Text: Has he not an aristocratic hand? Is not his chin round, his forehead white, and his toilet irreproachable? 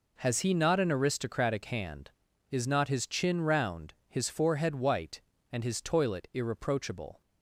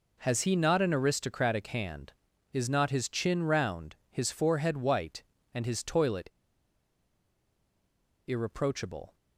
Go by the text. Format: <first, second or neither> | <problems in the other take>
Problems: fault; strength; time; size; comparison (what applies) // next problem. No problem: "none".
first | pauses between "toilet" and "irreproachable"; strong; at 6.2 s; 1.9 s long